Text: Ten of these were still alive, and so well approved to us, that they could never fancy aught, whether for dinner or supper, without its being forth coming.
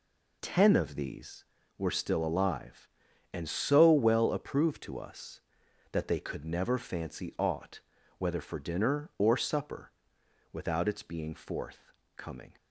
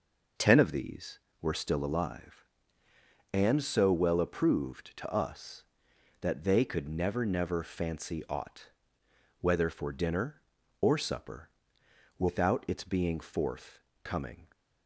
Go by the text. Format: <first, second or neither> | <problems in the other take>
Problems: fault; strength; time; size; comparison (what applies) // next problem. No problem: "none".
first | says "never" twice; at 7.2 s // pauses between "forth" and "coming"; slight; at 13.7 s; 0.22 s long; slight in the first